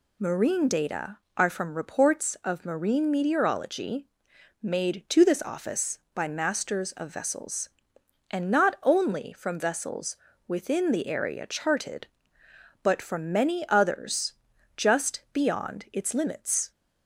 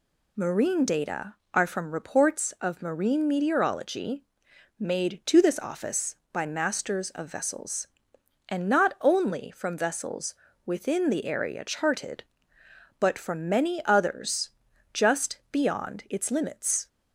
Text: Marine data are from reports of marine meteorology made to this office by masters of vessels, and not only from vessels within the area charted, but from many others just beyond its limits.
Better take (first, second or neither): neither